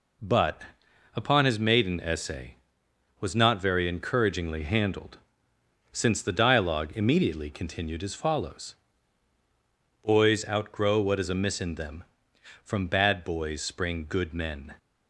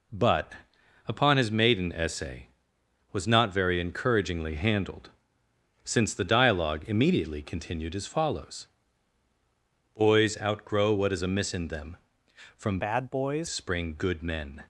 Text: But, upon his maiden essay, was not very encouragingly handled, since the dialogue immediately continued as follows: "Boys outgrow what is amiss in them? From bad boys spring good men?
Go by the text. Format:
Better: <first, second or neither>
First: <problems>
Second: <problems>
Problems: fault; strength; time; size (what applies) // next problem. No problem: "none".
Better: first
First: none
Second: changes voice from "bad" to "boys"; from 12.7 to 13.4 s; 0.7 s long